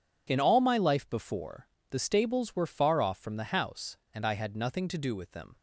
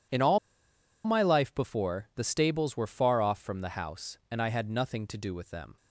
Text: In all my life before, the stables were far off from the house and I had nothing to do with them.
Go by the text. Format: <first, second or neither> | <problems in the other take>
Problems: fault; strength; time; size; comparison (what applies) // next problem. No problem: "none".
first | pauses between "all" and "my"; noticeable; at 0.3 s; 0.67 s long